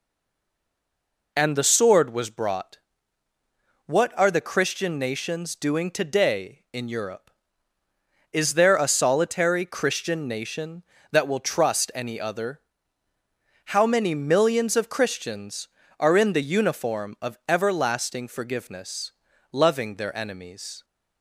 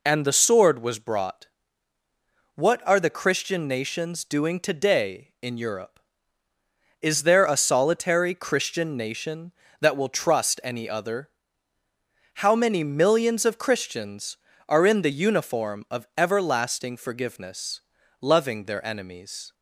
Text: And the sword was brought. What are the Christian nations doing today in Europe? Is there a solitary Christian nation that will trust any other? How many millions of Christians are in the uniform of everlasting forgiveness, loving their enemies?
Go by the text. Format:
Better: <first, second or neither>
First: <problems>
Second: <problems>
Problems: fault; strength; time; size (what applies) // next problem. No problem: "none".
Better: second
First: stays silent before the first word; noticeable; until 1.3 s; 1.3 s long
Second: none